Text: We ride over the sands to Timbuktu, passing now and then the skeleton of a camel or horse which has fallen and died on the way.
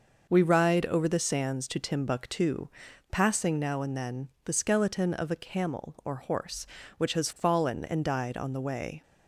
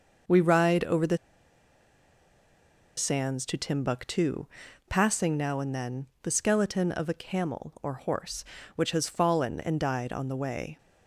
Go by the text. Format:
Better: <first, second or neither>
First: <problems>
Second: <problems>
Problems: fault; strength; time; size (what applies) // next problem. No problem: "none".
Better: first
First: pauses between "then" and "the"; slight; at 4.2 s; 0.16 s long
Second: pauses between "the" and "sands"; strong; at 1.1 s; 1.7 s long // pauses between "then" and "the"; slight; at 6.0 s; 0.16 s long